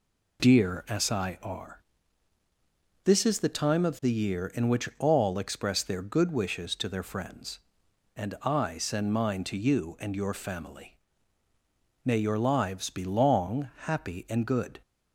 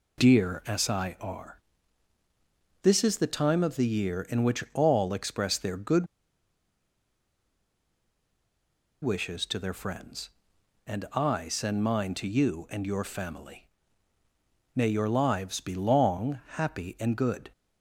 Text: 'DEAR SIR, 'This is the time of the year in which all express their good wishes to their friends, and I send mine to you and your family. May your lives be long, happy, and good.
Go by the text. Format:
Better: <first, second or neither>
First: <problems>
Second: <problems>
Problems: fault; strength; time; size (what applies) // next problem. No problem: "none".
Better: first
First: none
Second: pauses between "good" and "wishes"; strong; at 6.0 s; 2.9 s long